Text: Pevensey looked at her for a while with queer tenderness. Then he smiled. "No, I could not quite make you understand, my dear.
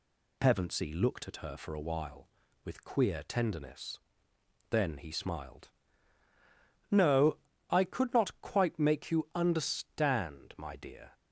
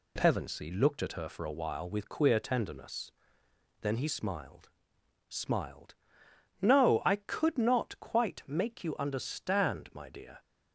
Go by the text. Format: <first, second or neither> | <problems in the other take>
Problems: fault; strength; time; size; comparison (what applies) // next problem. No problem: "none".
first | says "smiled" twice; at 5.2 s